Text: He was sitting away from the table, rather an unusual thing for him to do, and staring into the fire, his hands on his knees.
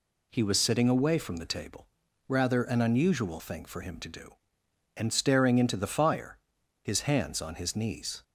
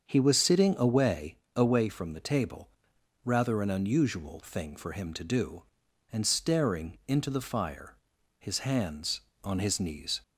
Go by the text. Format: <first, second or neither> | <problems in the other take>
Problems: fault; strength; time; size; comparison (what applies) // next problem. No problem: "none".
first | starts louder than the rest; until 1.0 s; 7 dB // says "away" twice; at 1.5 s